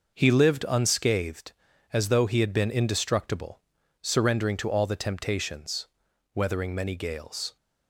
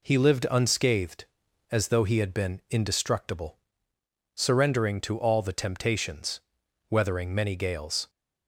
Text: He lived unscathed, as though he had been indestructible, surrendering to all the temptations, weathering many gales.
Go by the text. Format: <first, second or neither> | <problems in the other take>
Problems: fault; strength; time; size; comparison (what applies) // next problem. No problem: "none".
neither | none